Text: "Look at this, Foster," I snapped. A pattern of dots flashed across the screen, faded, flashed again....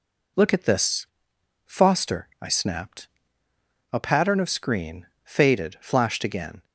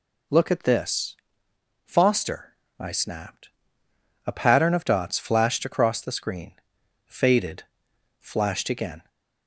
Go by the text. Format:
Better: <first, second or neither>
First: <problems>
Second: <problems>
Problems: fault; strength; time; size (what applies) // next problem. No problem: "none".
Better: second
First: skips "dots flashed across the"; at 4.4 s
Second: none